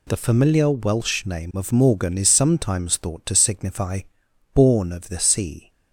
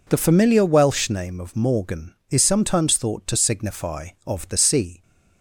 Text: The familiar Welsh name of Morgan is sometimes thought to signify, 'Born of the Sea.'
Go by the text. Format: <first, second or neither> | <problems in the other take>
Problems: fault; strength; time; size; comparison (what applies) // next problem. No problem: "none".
first | skips "Born"; at 4.1 s